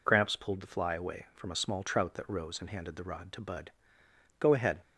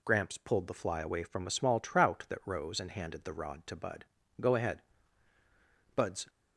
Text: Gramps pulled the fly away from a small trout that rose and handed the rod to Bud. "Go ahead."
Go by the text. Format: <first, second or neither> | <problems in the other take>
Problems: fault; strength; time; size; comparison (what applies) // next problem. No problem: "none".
first | goes on to say "Bud's"; slight; from 5.9 s on; 0.32 s long